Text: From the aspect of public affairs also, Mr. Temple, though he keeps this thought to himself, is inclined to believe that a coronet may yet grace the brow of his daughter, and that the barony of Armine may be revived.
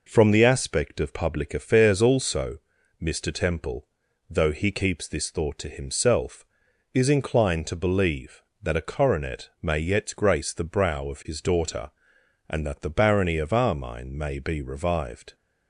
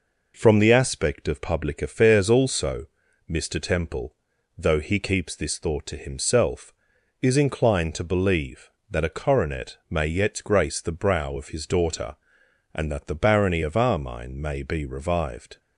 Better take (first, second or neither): neither